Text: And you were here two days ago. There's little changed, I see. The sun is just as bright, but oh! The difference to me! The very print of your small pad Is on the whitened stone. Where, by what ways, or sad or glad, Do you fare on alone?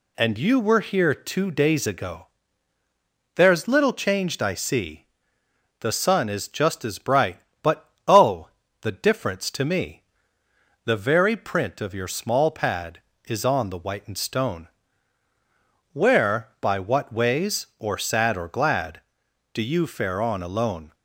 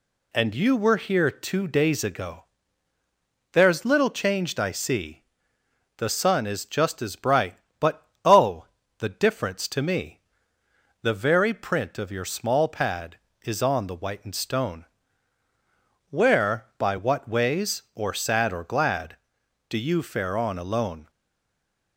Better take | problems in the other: first | pauses between "but" and "oh"; slight; at 8.0 s; 0.18 s long; slight in the first // stays silent after the last word; slight; from 21.0 s on; 0.9 s long

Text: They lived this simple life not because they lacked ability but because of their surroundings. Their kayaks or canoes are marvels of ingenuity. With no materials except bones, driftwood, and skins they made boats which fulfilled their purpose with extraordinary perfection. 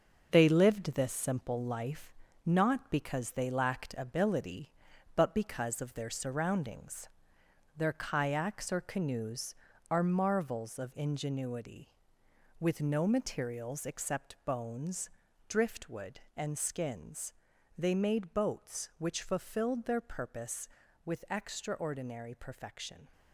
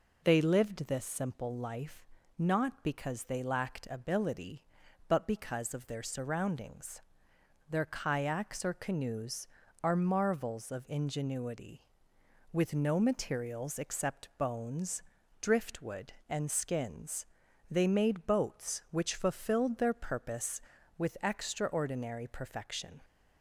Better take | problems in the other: second | gets quieter; throughout; 7 dB // pauses between "life" and "not"; slight; at 2.1 s; 0.32 s long; slight in the second // pauses between "skins" and "they"; noticeable; at 17.3 s; 0.46 s long; noticeable in the second

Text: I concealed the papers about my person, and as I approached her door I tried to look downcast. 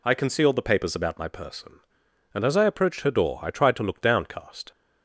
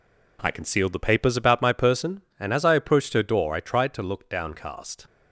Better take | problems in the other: neither | none

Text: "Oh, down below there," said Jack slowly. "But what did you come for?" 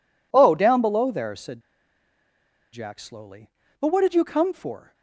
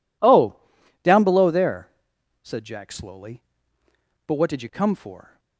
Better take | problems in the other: second | pauses between "said" and "Jack"; at 1.5 s; 1.1 s long

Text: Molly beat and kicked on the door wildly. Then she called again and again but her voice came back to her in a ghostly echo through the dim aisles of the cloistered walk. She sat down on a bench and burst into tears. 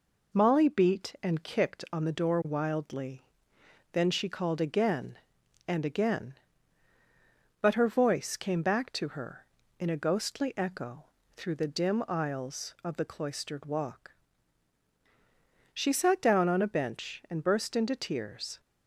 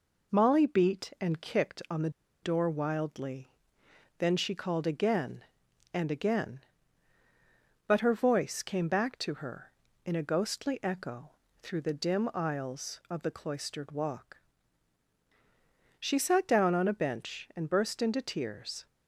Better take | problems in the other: first | pauses between "the" and "door"; slight; at 2.0 s; 0.33 s long // pauses between "echo" and "through"; slight; at 11.2 s; 0.30 s long; slight in the first

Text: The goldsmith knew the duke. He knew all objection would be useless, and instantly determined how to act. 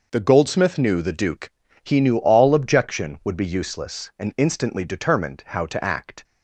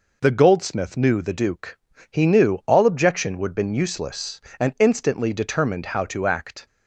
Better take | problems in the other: first | says "been" for "be"; at 3.5 s

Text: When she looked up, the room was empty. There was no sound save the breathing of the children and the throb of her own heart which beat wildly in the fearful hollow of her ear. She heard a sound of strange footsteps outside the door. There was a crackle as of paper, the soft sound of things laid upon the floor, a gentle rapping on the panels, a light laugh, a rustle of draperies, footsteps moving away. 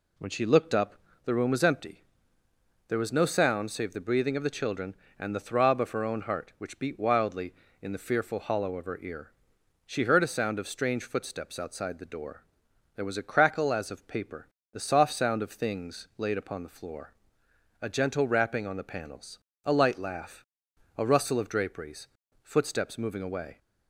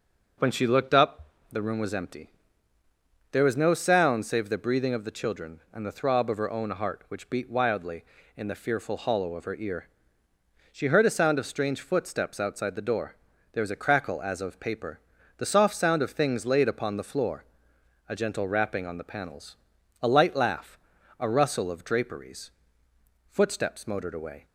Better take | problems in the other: first | says "motored" for "moving"; at 23.8 s

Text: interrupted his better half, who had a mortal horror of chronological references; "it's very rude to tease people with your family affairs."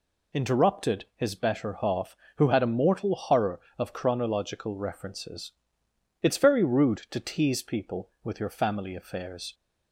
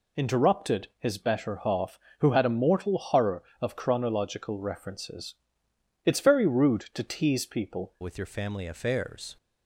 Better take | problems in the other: first | changes voice at "with"; from 8.0 s on; 1.3 s long

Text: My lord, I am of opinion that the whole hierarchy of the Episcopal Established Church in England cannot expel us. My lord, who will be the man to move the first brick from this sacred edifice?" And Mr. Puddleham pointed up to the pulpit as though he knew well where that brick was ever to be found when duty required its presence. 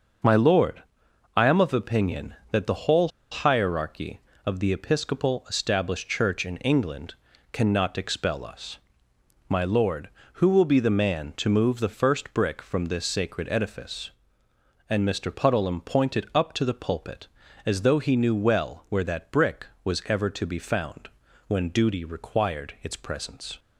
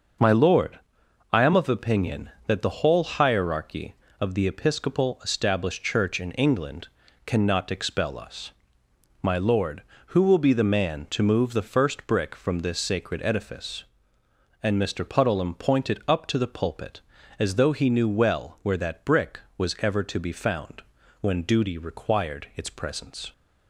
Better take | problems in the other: second | starts louder than the rest; until 1.7 s; 6.5 dB; noticeable in the second // pauses between "whole" and "hierarchy"; slight; at 3.0 s; 0.23 s long // pauses between "England" and "cannot"; at 7.1 s; 0.38 s long; also in the second // pauses between "found" and "when"; at 21.0 s; 0.40 s long; also in the second

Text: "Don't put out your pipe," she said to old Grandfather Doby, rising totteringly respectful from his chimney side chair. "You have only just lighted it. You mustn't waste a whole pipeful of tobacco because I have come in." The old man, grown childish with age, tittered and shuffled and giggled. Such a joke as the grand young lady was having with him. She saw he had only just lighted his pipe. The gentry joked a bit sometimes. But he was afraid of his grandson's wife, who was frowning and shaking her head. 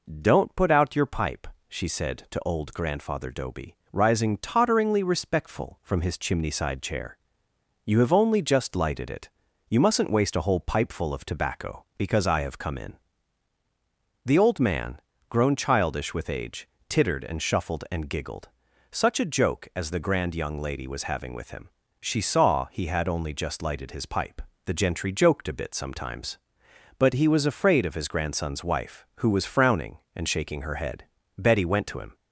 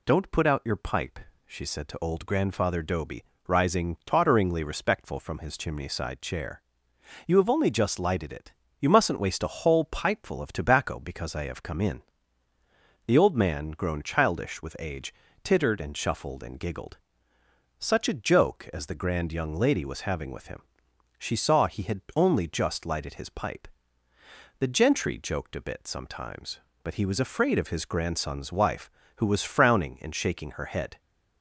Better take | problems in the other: second | goes on to say "Betty went to him"; noticeable; from 31.3 s on; 0.76 s long

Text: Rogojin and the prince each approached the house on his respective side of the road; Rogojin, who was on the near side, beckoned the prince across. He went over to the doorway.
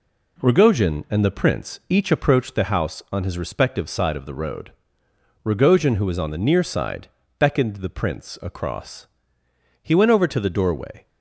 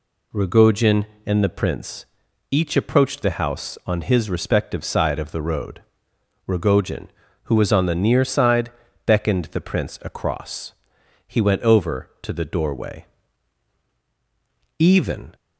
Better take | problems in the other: first | pauses between "prince" and "each"; noticeable; at 2.0 s; 0.46 s long // goes on to say "Even"; from 14.7 s on; 0.58 s long

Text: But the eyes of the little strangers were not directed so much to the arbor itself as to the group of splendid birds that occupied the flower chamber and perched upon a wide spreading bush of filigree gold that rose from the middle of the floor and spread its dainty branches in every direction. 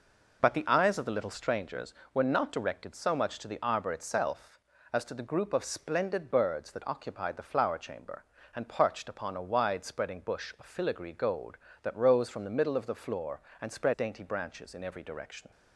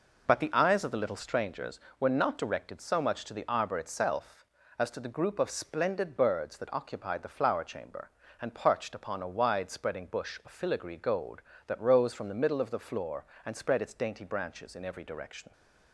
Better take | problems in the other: second | skips "its"; at 13.9 s

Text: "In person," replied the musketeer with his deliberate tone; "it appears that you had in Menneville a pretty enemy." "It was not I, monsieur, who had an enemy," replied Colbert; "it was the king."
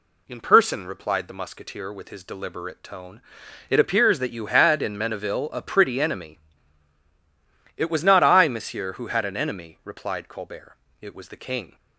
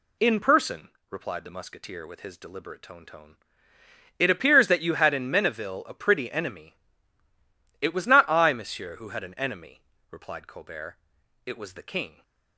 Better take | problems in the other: first | says "tone" twice; at 3.0 s

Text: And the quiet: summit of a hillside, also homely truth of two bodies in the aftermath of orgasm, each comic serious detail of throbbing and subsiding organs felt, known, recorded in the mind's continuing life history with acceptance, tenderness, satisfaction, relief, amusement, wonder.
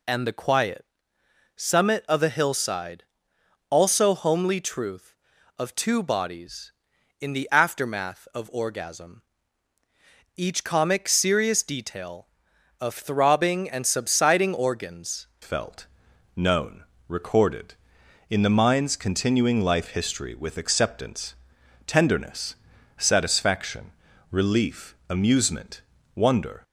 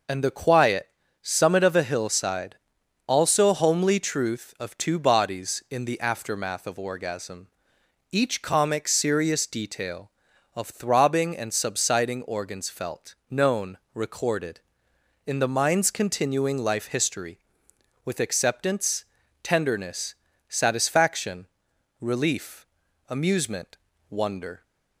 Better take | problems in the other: second | changes voice at "felt"; from 15.4 s on; 11.2 s long

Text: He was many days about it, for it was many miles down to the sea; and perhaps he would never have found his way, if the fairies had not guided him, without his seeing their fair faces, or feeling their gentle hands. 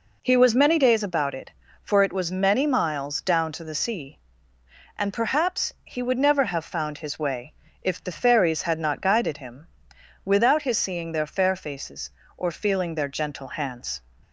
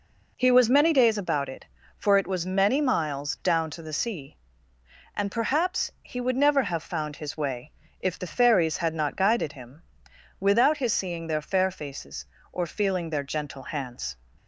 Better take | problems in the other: neither | none

